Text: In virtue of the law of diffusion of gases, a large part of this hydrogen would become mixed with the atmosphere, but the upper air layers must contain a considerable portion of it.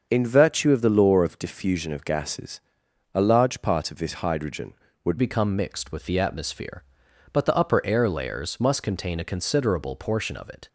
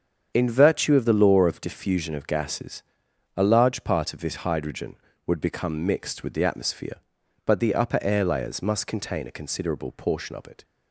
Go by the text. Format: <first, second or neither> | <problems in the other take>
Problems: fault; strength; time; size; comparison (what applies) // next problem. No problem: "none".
second | starts louder than the rest; until 1.1 s; 6.5 dB; strong in the second // changes voice at "become"; from 5.1 s on; 5.5 s long